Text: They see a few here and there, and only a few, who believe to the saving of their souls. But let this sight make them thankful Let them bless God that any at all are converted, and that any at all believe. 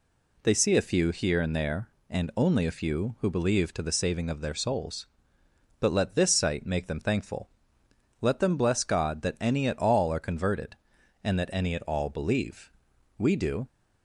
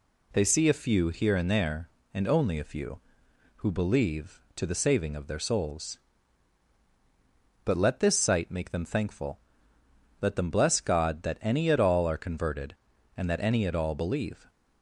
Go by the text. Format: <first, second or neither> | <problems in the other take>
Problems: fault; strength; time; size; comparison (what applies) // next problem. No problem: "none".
second | pauses between "thankful" and "Let"; noticeable; at 7.4 s; 0.72 s long; noticeable in the second // goes on to say "We do"; from 13.1 s on; 0.50 s long